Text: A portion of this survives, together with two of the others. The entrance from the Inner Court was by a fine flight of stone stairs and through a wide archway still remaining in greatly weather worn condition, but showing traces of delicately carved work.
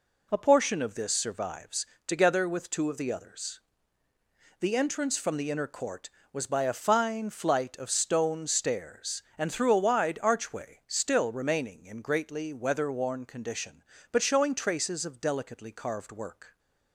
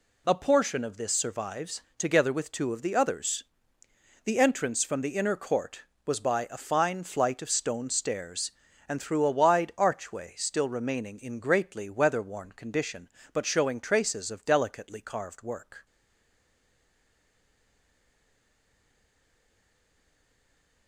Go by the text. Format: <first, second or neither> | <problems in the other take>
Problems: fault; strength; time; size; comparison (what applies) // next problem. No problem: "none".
first | stays silent after the last word; strong; from 15.8 s on; 5.0 s long